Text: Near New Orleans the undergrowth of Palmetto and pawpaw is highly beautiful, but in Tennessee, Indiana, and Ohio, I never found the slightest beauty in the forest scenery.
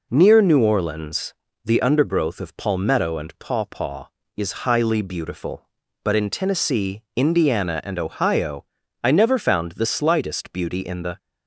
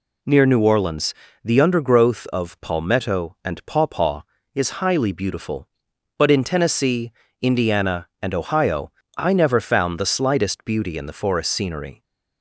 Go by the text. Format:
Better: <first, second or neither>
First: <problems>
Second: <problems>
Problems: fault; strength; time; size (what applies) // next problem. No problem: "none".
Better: second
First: pauses between "Orleans" and "the"; slight; at 1.3 s; 0.30 s long // stops before "forest scenery"; at 11.1 s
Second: pauses between "Orleans" and "the"; slight; at 1.1 s; 0.28 s long